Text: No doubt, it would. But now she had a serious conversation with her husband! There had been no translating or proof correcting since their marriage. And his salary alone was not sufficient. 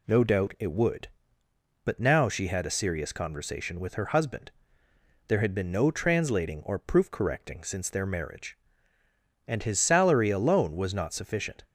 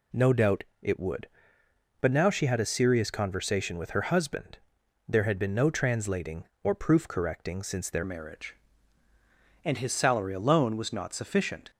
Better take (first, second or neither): first